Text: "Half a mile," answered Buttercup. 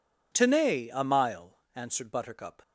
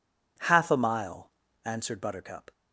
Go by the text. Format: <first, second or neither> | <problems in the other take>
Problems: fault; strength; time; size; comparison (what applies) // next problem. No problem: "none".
second | says "Tenay" for "Half"; at 0.3 s